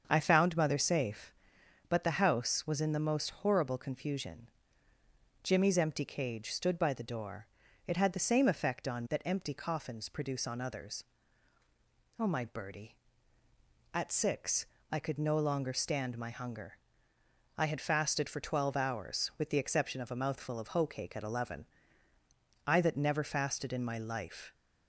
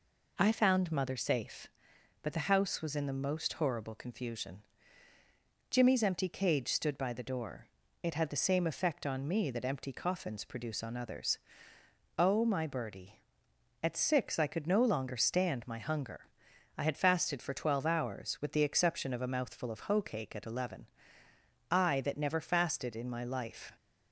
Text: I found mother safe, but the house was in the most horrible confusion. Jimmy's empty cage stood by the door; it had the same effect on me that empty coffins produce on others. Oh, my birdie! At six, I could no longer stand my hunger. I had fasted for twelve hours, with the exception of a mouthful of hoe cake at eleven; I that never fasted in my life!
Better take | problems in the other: second | starts louder than the rest; until 1.0 s; 7 dB // skips "me"; at 9.0 s

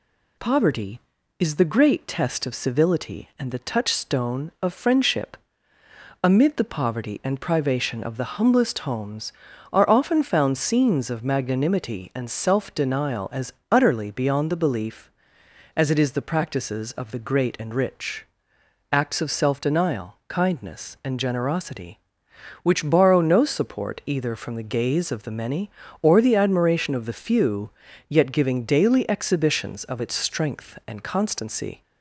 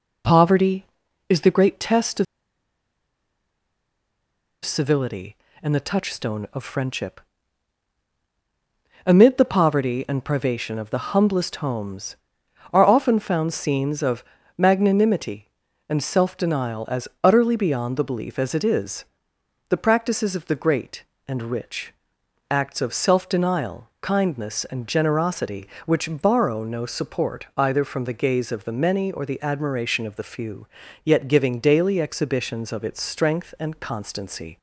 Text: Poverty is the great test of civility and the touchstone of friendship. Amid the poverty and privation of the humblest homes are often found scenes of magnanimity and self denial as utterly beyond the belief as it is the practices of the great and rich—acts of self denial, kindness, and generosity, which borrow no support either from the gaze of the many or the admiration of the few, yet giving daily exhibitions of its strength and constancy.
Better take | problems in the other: first | pauses between "of" and "civility"; strong; at 2.2 s; 2.4 s long // pauses between "of" and "magnanimity"; slight; at 14.2 s; 0.34 s long // pauses between "as" and "utterly"; slight; at 17.0 s; 0.16 s long; slight in the first // pauses between "is" and "the"; noticeable; at 19.0 s; 0.64 s long

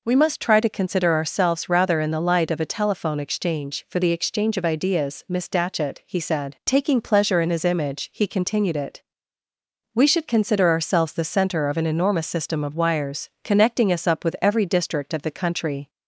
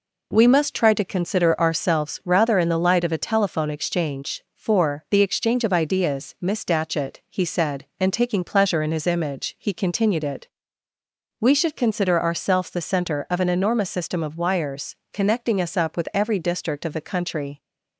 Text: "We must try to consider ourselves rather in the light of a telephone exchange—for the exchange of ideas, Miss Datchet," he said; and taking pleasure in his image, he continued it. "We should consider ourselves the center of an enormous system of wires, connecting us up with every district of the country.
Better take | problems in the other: second | skips "and"; at 6.6 s

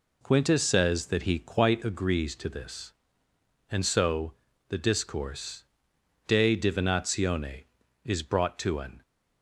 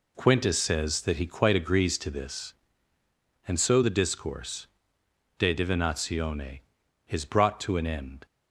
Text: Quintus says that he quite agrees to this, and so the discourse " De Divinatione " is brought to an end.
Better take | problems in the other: second | pauses between "so" and "the"; slight; at 4.3 s; 0.34 s long // stops before "end"; at 9.0 s

